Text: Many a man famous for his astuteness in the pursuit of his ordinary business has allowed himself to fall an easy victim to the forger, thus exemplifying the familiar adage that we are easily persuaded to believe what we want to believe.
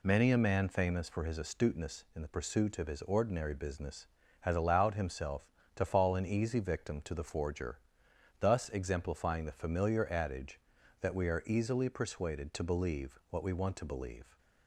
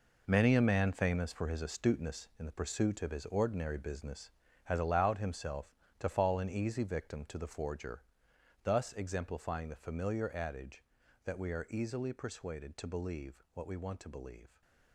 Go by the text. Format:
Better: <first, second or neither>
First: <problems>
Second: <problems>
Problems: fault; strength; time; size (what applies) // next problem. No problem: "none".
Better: first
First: none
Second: gets quieter; strong; throughout; 11.5 dB